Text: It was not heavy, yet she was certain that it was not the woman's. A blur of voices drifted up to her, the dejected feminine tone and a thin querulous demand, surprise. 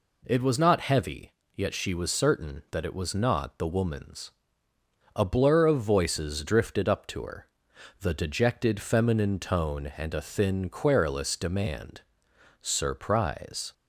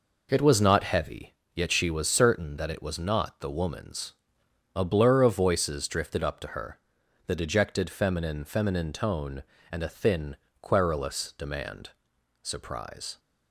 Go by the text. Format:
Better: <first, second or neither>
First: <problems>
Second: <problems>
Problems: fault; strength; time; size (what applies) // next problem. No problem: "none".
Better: first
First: none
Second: says "feminine" twice; at 8.4 s // pauses between "thin" and "querulous"; slight; at 10.3 s; 0.26 s long